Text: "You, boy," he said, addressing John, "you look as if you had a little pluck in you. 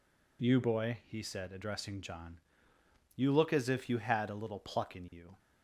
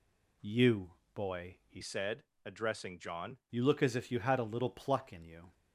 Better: first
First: none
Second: changes voice from "said" to "John"; from 1.8 to 3.3 s; 1.5 s long

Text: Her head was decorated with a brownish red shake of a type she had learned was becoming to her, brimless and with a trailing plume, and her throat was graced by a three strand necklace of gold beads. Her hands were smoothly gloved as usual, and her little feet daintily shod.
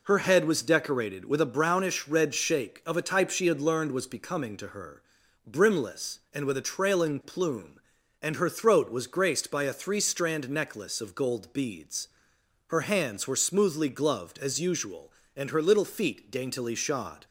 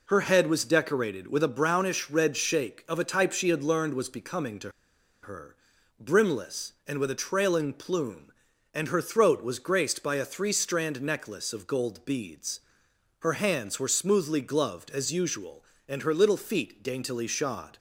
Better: first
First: none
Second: pauses between "to" and "her"; noticeable; at 4.7 s; 0.52 s long

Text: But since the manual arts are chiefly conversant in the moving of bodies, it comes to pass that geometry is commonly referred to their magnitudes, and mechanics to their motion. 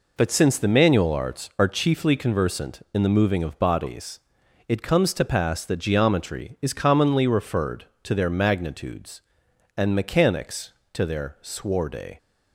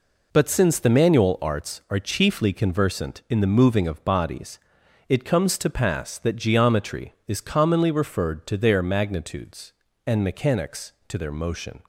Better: second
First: says "sworde" for "motion"; at 11.4 s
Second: none

